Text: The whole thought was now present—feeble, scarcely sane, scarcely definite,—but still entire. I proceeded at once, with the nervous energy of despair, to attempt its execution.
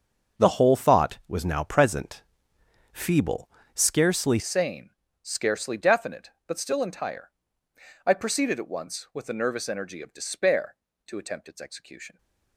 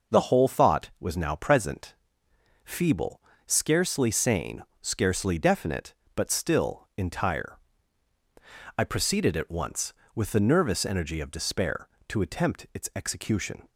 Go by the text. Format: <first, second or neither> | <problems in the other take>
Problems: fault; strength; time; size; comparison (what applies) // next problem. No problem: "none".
second | starts louder than the rest; until 1.4 s; 6.5 dB // changes voice at "sane"; from 4.3 s on; 7.8 s long